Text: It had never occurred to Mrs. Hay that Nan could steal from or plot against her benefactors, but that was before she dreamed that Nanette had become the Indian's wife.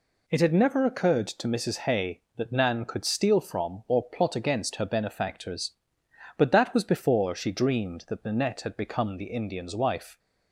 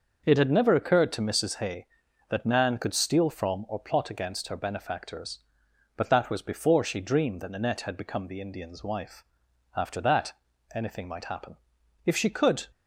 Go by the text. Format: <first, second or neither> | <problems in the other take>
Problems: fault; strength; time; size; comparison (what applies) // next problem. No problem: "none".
first | starts louder than the rest; noticeable; until 1.2 s; 6 dB // goes on to say "After that anything might happen If she could"; strong; from 9.7 s on; 2.9 s long